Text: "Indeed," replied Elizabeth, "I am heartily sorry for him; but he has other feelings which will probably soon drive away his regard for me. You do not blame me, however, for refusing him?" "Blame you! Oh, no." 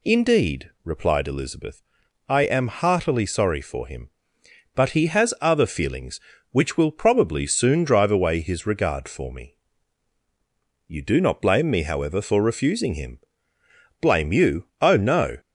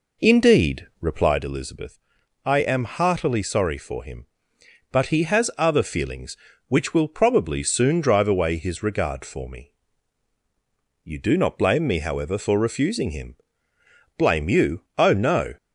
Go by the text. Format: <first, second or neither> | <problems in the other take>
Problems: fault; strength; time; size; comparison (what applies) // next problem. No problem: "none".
first | starts louder than the rest; noticeable; until 1.5 s; 4.5 dB